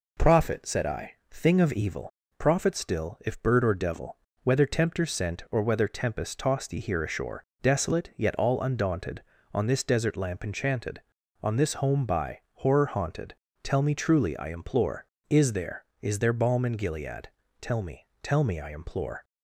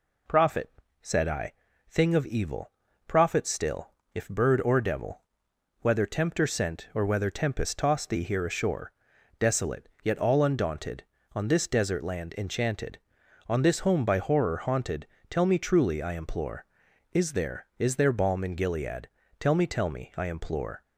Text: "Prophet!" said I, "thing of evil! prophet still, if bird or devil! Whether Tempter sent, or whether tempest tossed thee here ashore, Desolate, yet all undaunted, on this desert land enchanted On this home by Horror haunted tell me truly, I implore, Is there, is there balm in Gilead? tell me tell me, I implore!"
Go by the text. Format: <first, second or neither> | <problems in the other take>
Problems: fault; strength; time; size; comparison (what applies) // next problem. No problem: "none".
second | says "lamp" for "land"; at 10.1 s // pauses between "haunted" and "tell"; slight; at 13.3 s; 0.26 s long; slight in the second // pauses between "me" and "tell"; slight; at 18.0 s; 0.16 s long